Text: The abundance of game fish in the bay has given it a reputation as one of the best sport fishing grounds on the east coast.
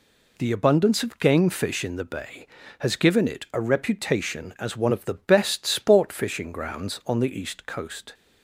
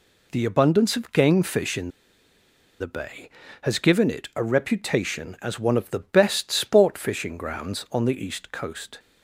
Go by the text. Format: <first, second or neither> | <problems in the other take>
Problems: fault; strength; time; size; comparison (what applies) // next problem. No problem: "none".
first | pauses between "in" and "the"; noticeable; at 1.8 s; 0.90 s long